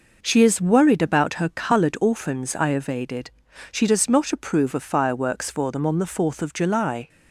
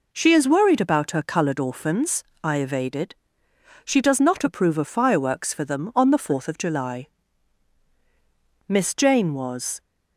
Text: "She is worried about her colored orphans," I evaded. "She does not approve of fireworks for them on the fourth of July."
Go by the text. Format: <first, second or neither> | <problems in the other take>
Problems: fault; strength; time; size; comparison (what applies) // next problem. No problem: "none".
first | goes on to say "Miss Jane was"; noticeable; from 8.6 s on; 1.1 s long